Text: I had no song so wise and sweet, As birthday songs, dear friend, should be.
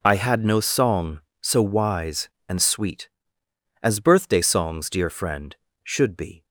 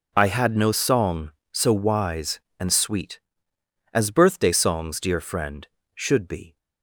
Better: neither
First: none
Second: none

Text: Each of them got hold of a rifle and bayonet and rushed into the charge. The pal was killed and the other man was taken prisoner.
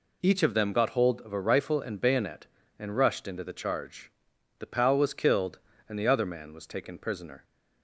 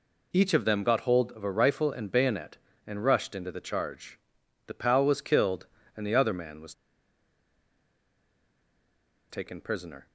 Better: first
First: none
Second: pauses between "was" and "taken"; strong; at 6.7 s; 2.5 s long

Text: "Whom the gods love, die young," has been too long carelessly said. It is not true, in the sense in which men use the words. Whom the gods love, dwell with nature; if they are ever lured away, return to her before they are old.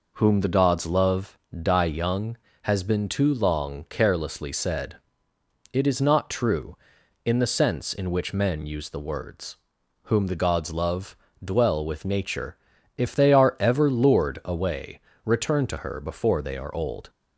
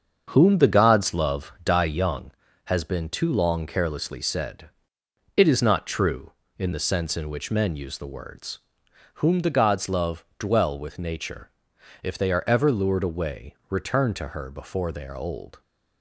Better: first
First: none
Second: starts louder than the rest; until 2.2 s; 7 dB

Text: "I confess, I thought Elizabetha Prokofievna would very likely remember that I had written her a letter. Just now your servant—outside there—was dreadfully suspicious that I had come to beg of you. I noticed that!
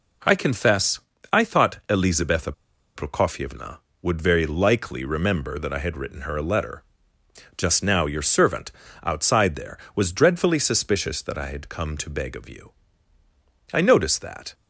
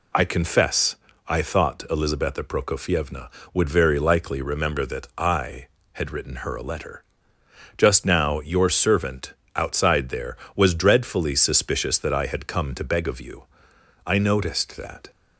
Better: second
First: pauses between "Elizabetha" and "Prokofievna"; at 2.5 s; 0.43 s long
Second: none

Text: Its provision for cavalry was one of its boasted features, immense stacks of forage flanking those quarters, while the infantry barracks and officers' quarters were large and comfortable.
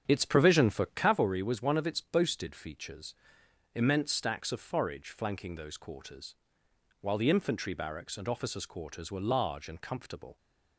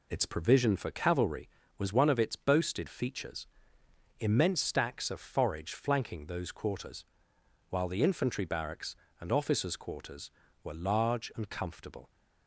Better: second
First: starts louder than the rest; strong; until 1.2 s; 8.5 dB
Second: none

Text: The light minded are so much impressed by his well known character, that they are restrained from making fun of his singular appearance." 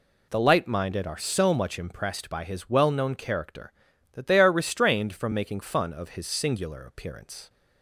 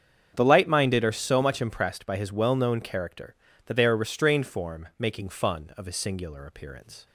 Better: first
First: none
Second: starts louder than the rest; strong; until 1.3 s; 7.5 dB // says "form" for "from"; at 4.4 s

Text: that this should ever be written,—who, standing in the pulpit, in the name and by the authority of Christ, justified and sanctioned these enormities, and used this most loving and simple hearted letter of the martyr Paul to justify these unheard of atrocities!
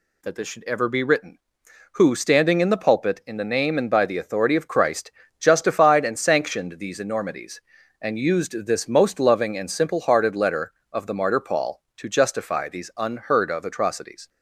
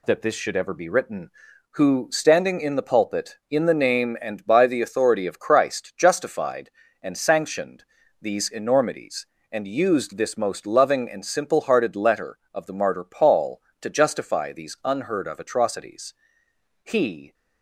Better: first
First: none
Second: pauses between "sanctioned" and "these"; at 7.8 s; 0.38 s long // goes on to say "He"; from 16.8 s on; 0.50 s long

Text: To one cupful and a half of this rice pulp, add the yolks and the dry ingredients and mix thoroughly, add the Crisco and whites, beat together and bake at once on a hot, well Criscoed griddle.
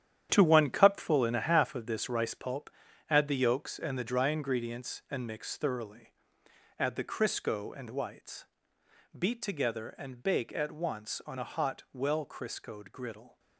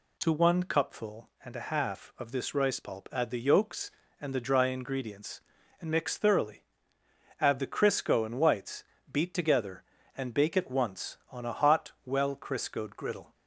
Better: second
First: gets quieter; strong; throughout; 10 dB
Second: none

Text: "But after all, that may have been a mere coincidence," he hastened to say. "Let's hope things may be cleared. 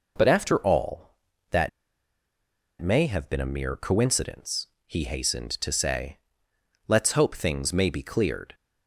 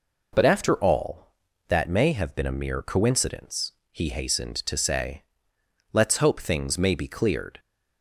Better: second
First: pauses between "that" and "may"; at 1.6 s; 1.1 s long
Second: none

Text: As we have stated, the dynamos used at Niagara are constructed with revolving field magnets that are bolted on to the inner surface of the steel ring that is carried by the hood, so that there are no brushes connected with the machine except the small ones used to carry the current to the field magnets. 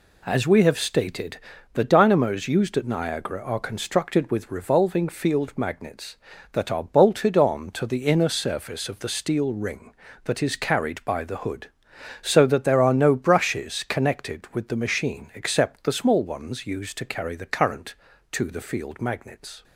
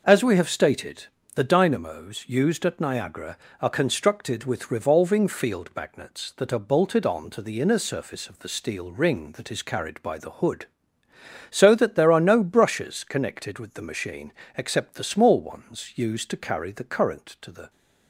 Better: first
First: none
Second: pauses between "machine" and "except"; slight; at 14.3 s; 0.24 s long // stops before "field magnets"; at 17.6 s

